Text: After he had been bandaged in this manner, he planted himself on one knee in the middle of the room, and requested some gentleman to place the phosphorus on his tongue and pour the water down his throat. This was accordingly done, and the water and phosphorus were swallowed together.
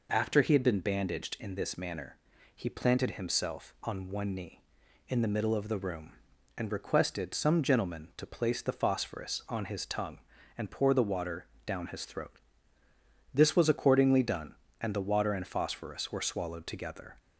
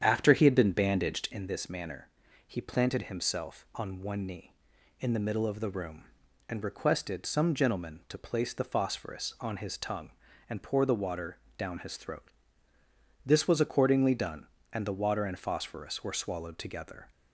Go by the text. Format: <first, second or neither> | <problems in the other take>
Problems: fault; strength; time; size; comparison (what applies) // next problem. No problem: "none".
first | starts louder than the rest; strong; until 1.5 s; 9 dB // pauses between "water" and "down"; slight; at 11.3 s; 0.18 s long; slight in the first